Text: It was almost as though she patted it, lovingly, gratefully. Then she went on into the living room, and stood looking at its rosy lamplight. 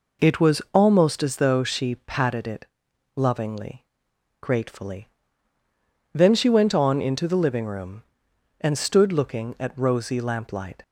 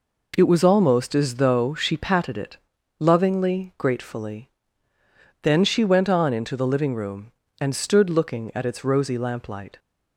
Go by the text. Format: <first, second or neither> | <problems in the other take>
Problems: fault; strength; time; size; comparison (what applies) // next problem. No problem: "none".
second | skips "its"; at 9.7 s